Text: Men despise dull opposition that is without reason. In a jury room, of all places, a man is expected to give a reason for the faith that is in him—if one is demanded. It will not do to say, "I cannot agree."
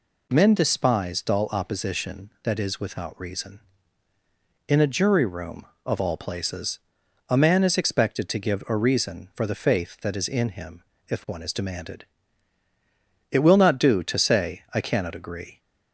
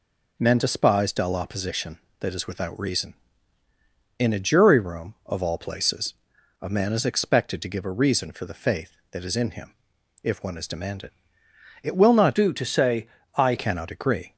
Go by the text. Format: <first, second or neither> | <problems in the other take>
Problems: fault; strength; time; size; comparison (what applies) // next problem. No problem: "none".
first | changes voice from "do" to "I"; from 12.3 to 13.5 s; 1.2 s long